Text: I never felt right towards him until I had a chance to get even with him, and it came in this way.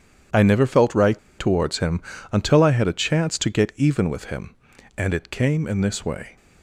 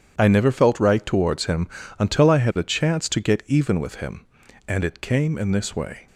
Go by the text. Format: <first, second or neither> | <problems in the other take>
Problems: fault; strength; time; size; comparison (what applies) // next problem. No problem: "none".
second | starts louder than the rest; strong; until 1.5 s; 9 dB; strong in the second // pauses between "right" and "towards"; slight; at 1.1 s; 0.18 s long // pauses between "him" and "until"; slight; at 1.9 s; 0.32 s long; slight in the second